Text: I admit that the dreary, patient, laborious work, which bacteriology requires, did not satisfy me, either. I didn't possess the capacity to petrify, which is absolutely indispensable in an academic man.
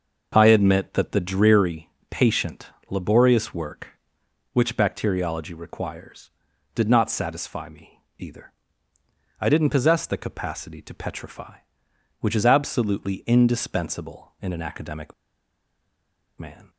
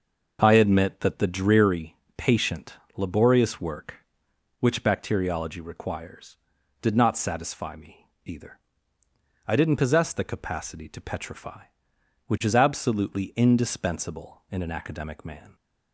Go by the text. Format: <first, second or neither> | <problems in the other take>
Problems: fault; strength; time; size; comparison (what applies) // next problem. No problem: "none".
second | pauses between "academic" and "man"; strong; at 15.1 s; 1.2 s long